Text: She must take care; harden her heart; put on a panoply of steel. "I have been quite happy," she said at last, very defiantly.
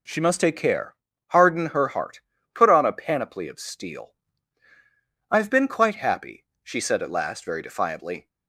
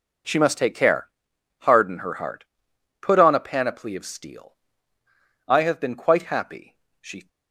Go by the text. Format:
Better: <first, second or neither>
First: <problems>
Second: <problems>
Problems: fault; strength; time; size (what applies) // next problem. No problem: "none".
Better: first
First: none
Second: stops before "said at last very defiantly"; at 7.2 s